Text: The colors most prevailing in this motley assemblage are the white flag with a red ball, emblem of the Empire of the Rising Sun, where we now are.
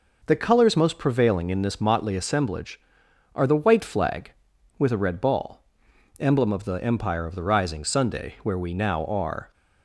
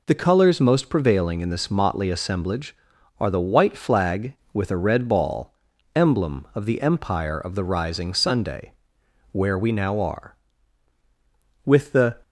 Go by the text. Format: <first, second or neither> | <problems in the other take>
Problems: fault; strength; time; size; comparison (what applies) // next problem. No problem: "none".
first | goes on to say "With the"; from 11.6 s on; 0.58 s long